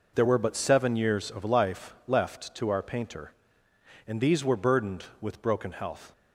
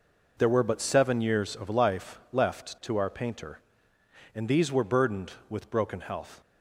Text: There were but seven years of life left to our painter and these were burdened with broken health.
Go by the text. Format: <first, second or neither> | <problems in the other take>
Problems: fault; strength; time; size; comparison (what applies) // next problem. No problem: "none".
neither | none